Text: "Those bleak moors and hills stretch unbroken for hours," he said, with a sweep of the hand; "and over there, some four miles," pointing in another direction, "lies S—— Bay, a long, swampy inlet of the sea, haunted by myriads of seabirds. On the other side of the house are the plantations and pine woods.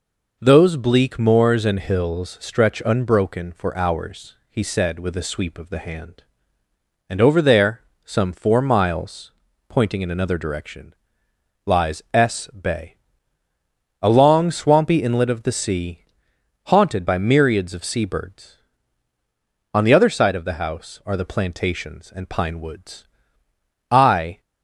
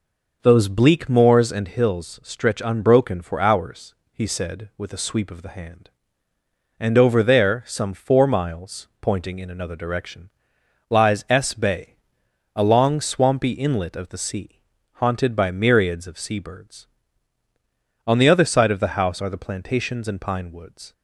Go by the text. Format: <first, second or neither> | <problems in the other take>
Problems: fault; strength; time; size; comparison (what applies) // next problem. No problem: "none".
second | goes on to say "I"; from 23.8 s on; 0.52 s long